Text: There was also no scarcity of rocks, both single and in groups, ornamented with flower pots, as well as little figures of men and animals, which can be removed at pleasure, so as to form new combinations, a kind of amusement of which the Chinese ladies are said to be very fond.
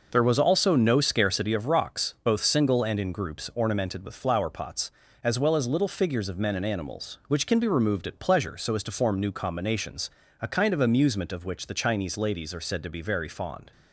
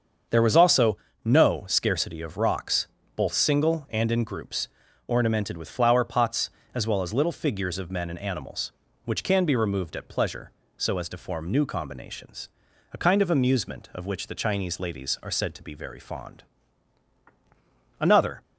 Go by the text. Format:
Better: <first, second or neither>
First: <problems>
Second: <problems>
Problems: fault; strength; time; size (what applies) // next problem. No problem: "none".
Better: first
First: none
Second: starts louder than the rest; until 1.5 s; 7 dB // pauses between "also" and "no"; slight; at 0.9 s; 0.28 s long // goes on to say "Another"; slight; from 18.0 s on; 0.42 s long